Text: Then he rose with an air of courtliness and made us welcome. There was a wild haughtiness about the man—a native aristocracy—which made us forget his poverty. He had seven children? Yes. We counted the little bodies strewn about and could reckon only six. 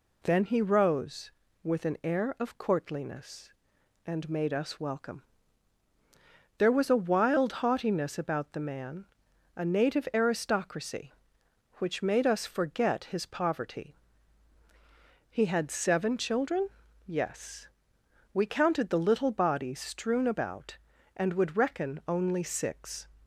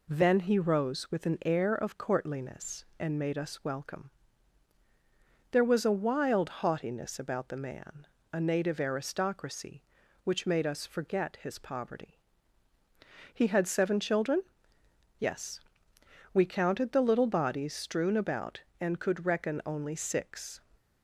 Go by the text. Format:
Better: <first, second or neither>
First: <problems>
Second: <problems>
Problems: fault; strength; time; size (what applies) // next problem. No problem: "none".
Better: second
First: says "would" for "could"; at 21.3 s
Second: none